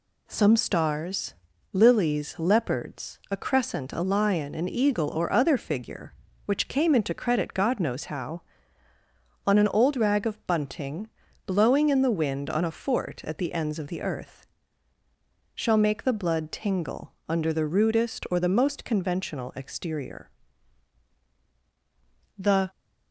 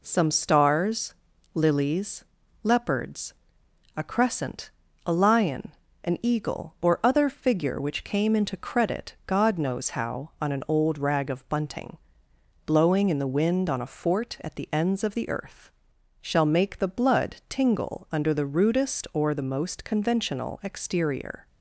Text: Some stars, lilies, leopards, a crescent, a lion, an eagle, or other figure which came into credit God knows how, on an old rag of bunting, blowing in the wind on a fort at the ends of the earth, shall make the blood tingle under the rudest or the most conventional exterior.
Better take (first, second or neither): second